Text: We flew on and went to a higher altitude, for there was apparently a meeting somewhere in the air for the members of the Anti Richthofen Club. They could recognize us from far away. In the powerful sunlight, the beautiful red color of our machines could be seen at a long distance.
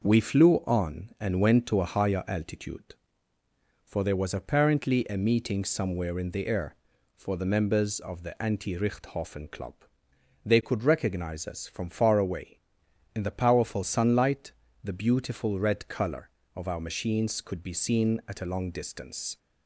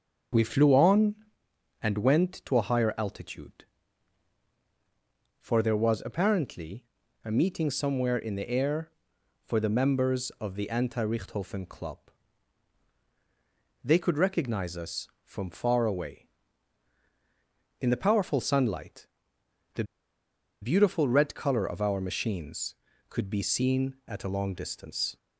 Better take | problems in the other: first | starts louder than the rest; until 2.0 s; 6.5 dB // pauses between "apparently" and "a"; at 6.8 s; 0.38 s long // pauses between "the" and "beautiful"; noticeable; at 19.8 s; 0.78 s long

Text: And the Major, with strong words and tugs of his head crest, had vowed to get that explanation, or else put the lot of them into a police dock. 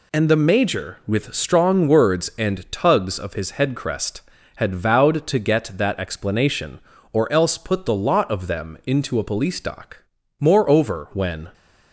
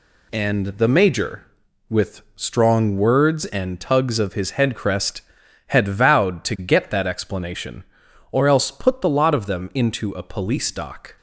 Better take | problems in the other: second | goes on to say "Moreover when"; noticeable; from 10.3 s on; 1.1 s long

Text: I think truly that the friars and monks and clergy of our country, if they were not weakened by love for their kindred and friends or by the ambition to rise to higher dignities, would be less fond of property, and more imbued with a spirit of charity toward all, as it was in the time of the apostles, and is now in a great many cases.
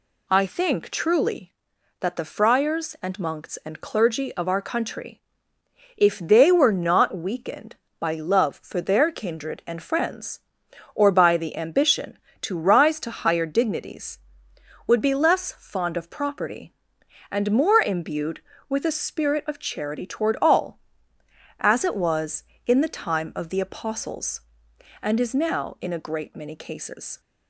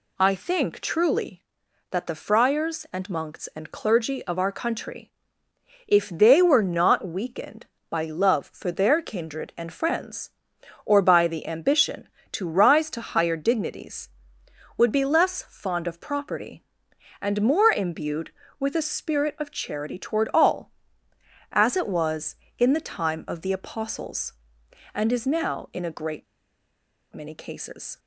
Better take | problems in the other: first | pauses between "great" and "many"; noticeable; at 26.2 s; 0.88 s long

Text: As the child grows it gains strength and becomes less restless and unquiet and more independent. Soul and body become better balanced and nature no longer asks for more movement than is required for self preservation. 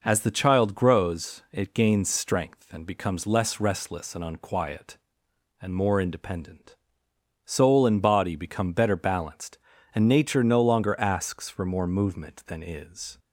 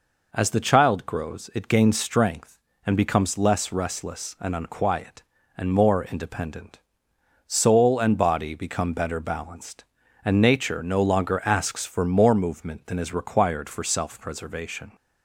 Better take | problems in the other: second | stops before "required for self preservation"; at 13.1 s

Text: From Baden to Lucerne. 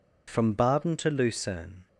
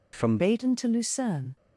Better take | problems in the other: first | changes voice at "Baden"; from 0.3 s on; 1.2 s long

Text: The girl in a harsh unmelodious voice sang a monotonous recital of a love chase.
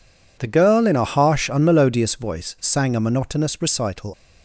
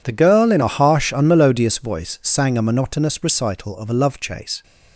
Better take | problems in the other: second | stops before "of a love chase"; at 4.1 s

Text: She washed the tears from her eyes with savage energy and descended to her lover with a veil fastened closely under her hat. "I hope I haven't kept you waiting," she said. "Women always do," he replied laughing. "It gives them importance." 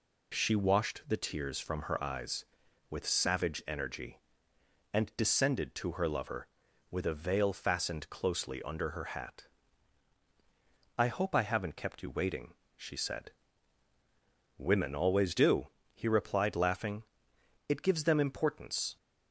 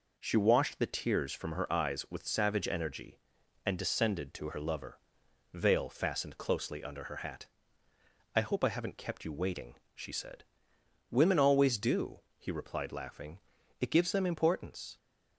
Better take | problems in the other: first | skips "with a"; at 5.2 s

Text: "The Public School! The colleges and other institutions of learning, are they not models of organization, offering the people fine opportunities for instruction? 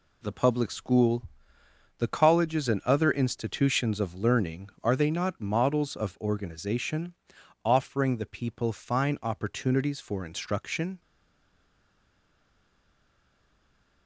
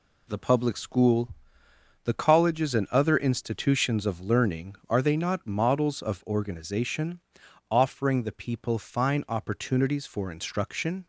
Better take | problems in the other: second | stays silent after the last word; strong; from 11.0 s on; 3.0 s long

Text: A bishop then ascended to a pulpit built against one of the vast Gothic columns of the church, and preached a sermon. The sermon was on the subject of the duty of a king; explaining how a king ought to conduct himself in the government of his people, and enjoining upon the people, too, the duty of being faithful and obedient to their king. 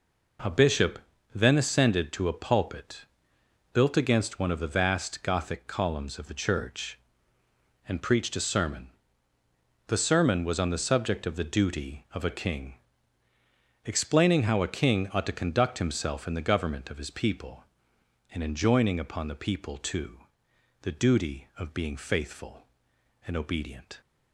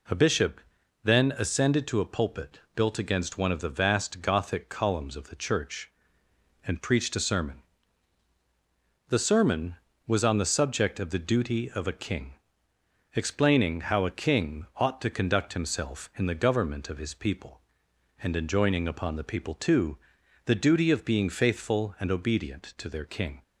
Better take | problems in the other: second | pauses between "bishop" and "then"; slight; at 0.9 s; 0.36 s long; also in the second // pauses between "pulpit" and "built"; noticeable; at 3.0 s; 0.70 s long; slight in the second // stops before "to their king"; at 24.0 s

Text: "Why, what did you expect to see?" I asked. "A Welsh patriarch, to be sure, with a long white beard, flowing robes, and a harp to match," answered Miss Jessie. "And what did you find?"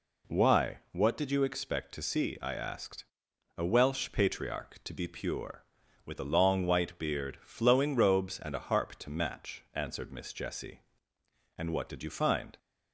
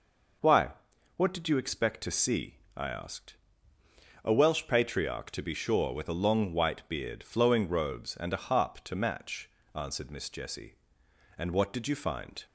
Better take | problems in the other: second | says "pure" for "sure"; at 5.0 s

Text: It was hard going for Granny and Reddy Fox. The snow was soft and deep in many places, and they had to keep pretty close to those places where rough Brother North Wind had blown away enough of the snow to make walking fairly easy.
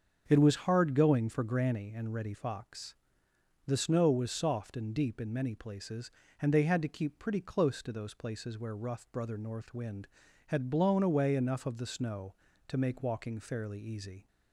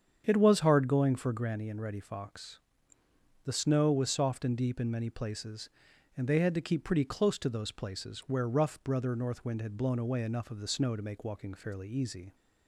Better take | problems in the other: neither | starts louder than the rest; strong; the same in both

